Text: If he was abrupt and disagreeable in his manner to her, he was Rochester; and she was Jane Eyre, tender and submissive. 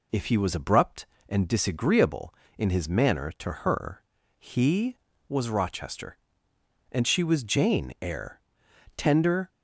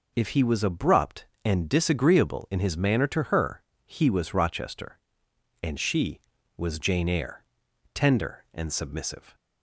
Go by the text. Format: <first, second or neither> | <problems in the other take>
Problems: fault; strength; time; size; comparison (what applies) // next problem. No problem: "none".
second | stops before "and submissive"; at 9.4 s